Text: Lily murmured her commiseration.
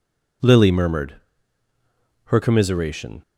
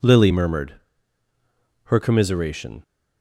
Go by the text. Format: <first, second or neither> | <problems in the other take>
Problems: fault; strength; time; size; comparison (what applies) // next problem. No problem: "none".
neither | pauses between "murmured" and "her"; the same in both